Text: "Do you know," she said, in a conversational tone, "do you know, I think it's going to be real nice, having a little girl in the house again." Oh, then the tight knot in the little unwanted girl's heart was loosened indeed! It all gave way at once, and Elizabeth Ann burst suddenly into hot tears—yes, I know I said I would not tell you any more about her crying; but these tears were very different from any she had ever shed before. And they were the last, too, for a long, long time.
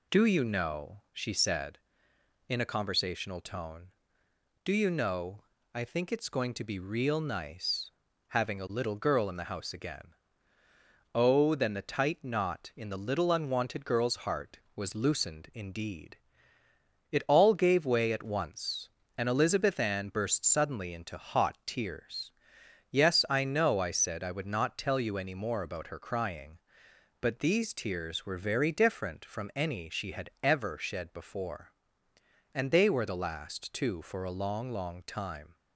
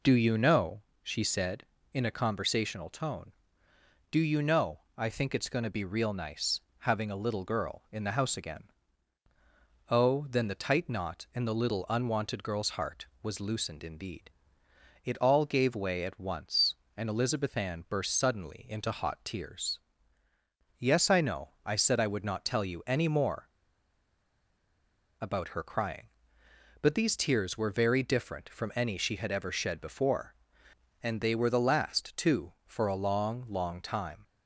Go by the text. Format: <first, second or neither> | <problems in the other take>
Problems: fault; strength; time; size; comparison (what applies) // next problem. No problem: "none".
first | pauses between "more" and "about"; strong; at 23.4 s; 1.6 s long